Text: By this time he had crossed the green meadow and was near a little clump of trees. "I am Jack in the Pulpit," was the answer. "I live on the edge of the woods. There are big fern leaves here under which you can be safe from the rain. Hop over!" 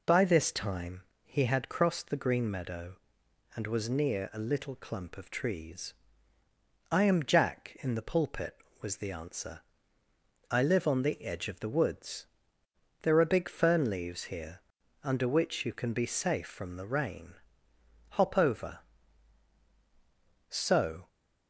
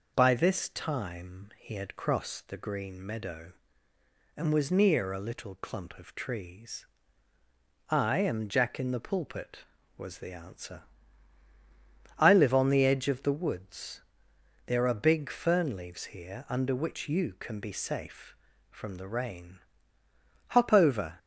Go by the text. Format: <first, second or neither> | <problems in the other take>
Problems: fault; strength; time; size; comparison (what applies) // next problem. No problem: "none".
second | pauses between "time" and "he"; slight; at 1.0 s; 0.22 s long // pauses between "here" and "under"; at 14.5 s; 0.42 s long // goes on to say "So"; from 20.4 s on; 0.58 s long